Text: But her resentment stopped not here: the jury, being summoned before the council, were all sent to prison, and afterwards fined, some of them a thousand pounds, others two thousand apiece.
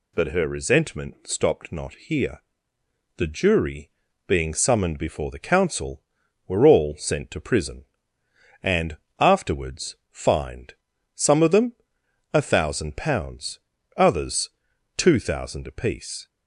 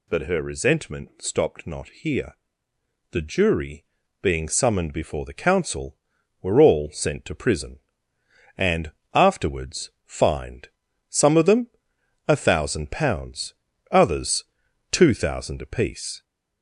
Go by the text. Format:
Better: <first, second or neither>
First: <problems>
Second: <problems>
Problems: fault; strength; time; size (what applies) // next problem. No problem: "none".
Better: first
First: pauses between "and" and "afterwards"; slight; at 8.9 s; 0.22 s long // pauses between "them" and "a"; noticeable; at 11.7 s; 0.60 s long // pauses between "others" and "two"; noticeable; at 14.5 s; 0.46 s long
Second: gets louder; noticeable; throughout; 4.5 dB // pauses between "and" and "afterwards"; slight; at 8.9 s; 0.22 s long // pauses between "them" and "a"; noticeable; at 11.6 s; 0.60 s long // pauses between "others" and "two"; noticeable; at 14.4 s; 0.46 s long